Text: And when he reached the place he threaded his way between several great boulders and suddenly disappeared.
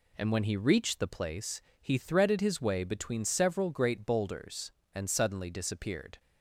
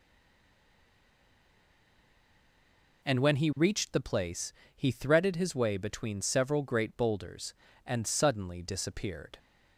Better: first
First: pauses between "place" and "he"; slight; at 1.6 s; 0.20 s long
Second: stays silent before the first word; strong; until 3.0 s; 3.0 s long // pauses between "place" and "he"; slight; at 4.5 s; 0.22 s long

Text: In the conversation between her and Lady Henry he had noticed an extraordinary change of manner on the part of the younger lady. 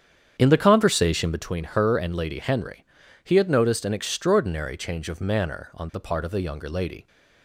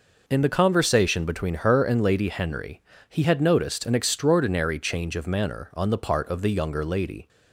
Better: second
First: starts louder than the rest; strong; until 1.4 s; 8.5 dB // pauses between "Henry" and "he"; at 2.8 s; 0.38 s long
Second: pauses between "Henry" and "he"; slight; at 2.8 s; 0.28 s long

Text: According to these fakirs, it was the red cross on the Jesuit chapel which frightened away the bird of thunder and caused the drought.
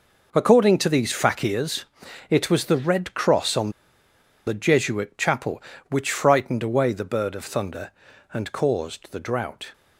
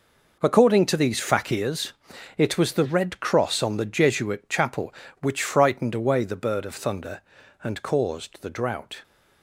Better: second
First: pauses between "on" and "the"; noticeable; at 3.7 s; 0.74 s long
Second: none

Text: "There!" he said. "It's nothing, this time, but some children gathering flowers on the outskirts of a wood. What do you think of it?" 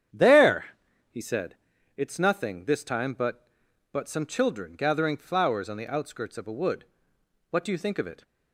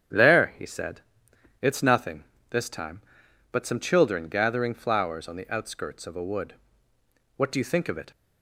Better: second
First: starts louder than the rest; strong; until 1.9 s; 9 dB // says "but" twice; at 3.9 s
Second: starts louder than the rest; strong; until 1.8 s; 9.5 dB

